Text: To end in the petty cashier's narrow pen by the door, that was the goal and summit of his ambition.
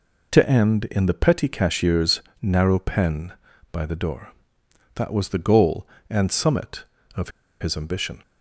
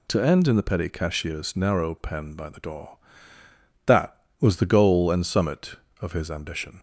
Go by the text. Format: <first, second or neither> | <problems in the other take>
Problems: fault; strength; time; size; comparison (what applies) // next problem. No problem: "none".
second | pauses between "cashier's" and "narrow"; slight; at 2.2 s; 0.18 s long // pauses between "of" and "his"; slight; at 7.2 s; 0.30 s long